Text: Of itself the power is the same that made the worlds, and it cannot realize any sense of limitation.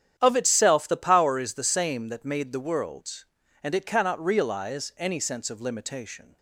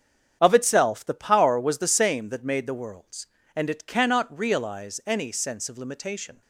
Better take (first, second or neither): first